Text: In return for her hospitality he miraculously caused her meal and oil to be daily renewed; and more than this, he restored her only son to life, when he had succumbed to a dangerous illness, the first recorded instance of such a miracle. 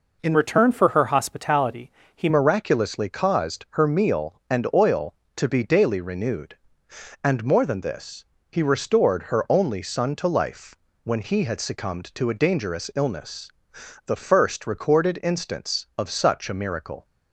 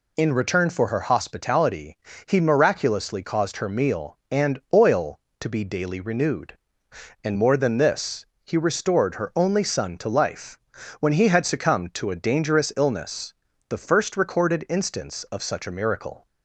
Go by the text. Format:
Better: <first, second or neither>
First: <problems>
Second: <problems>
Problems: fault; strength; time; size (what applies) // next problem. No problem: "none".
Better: second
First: changes voice from "return" to "he"; from 0.3 to 2.2 s; 1.9 s long // pauses between "hospitality" and "he"; slight; at 1.9 s; 0.24 s long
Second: pauses between "hospitality" and "he"; slight; at 1.9 s; 0.32 s long